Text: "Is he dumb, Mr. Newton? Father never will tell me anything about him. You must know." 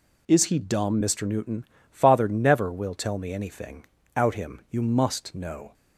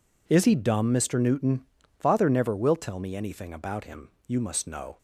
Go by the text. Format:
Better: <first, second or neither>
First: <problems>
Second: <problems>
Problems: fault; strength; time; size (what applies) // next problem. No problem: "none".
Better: second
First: says "out" for "about"; at 4.1 s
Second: none